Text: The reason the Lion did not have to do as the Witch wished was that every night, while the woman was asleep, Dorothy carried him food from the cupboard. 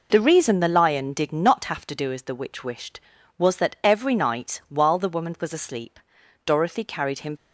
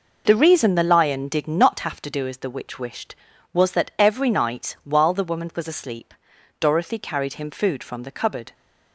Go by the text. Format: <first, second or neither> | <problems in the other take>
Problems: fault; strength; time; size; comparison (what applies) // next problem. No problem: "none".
second | stops before "food from the cupboard"; at 7.3 s